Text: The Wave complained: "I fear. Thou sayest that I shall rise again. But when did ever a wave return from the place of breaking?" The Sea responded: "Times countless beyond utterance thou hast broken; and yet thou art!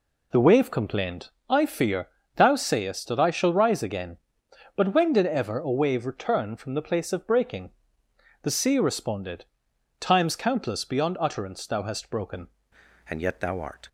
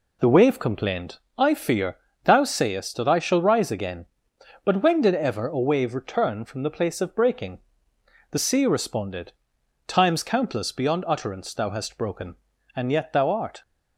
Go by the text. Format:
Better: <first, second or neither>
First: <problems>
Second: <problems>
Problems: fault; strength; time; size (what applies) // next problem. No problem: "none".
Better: second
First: changes voice at "and"; from 13.0 s on; 0.8 s long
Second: none